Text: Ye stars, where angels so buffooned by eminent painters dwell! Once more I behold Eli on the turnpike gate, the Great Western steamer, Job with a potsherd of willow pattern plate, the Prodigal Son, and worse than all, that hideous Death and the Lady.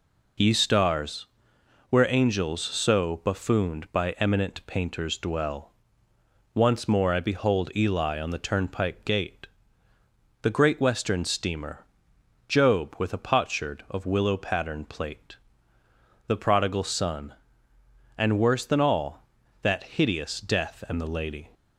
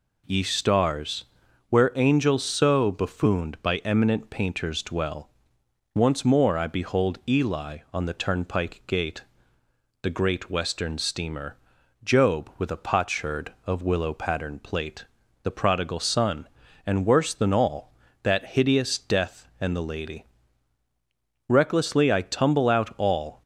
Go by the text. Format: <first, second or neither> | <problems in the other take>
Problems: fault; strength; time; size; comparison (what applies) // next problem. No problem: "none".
first | goes on to say "Recklessly I tumble out all"; strong; from 21.4 s on; 1.9 s long